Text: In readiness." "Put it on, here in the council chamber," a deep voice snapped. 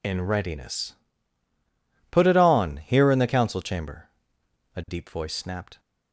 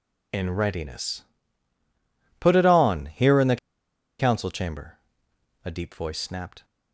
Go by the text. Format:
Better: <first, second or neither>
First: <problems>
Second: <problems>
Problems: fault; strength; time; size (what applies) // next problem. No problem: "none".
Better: first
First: none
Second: pauses between "the" and "council"; noticeable; at 3.5 s; 0.63 s long